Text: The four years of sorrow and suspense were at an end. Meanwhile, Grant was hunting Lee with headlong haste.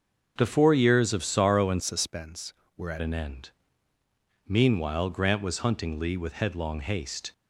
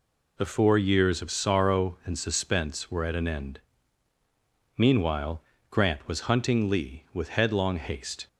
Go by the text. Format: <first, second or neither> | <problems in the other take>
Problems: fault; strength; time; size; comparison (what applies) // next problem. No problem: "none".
second | starts louder than the rest; until 1.3 s; 6.5 dB // changes voice from "suspense" to "at"; from 1.8 to 3.0 s; 1.2 s long